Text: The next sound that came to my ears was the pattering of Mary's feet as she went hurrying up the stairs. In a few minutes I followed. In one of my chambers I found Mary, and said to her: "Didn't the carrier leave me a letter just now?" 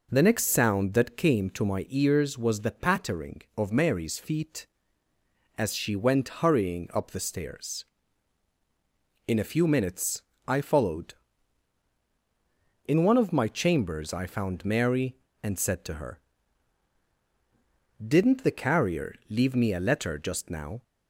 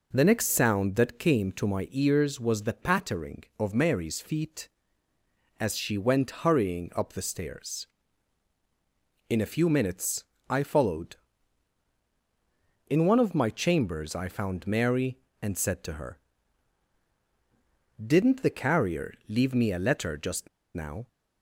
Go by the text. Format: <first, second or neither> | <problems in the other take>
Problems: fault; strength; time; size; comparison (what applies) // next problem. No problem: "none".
first | pauses between "minutes" and "I"; slight; at 10.2 s; 0.24 s long; slight in the first // pauses between "carrier" and "leave"; slight; at 19.1 s; 0.16 s long; slight in the first // pauses between "just" and "now"; slight; at 20.4 s; 0.27 s long